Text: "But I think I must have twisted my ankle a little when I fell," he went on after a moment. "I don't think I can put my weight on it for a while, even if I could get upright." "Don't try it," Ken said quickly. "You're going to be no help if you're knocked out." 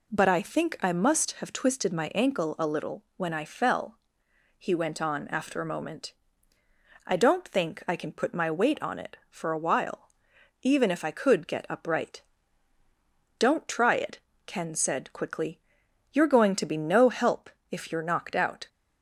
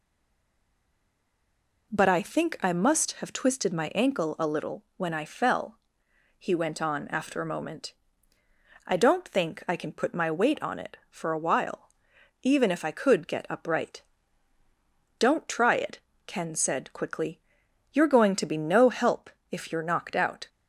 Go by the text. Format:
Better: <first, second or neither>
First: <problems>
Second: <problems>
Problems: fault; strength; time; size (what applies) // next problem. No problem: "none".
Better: first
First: pauses between "help" and "if"; slight; at 17.4 s; 0.20 s long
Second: stays silent before the first word; noticeable; until 1.9 s; 1.9 s long // pauses between "help" and "if"; slight; at 19.3 s; 0.20 s long